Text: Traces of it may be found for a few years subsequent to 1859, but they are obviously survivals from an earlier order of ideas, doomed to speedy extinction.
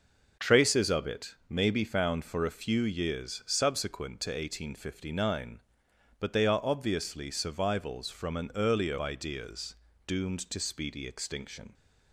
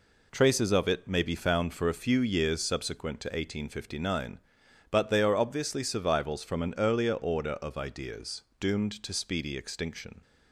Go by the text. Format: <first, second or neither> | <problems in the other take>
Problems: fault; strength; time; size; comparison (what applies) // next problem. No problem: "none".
second | skips "order of"; at 8.9 s